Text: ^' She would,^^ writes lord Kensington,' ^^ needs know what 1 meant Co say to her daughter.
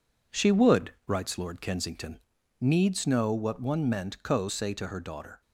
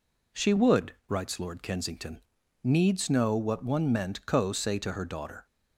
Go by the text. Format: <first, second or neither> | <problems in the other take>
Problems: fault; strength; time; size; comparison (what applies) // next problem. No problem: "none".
second | gets quieter; noticeable; throughout; 5.5 dB